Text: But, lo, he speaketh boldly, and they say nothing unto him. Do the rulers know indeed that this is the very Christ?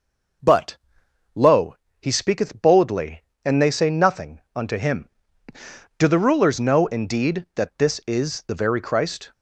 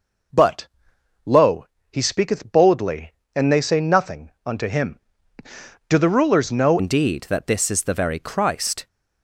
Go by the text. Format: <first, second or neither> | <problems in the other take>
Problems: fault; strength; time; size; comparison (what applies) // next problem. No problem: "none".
first | pauses between "nothing" and "unto"; slight; at 4.3 s; 0.16 s long; slight in the first // changes voice at "indeed"; from 6.7 s on; 2.1 s long